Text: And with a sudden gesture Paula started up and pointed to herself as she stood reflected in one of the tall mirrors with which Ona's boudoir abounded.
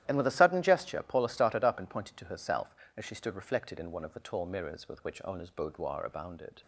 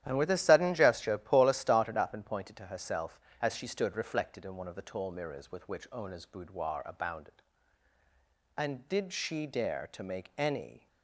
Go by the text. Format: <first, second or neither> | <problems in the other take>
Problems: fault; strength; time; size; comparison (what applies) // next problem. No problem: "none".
first | starts louder than the rest; strong; until 1.0 s; 12 dB; strong in the first // goes on to say "And did she dare to make any"; strong; from 8.5 s on; 2.3 s long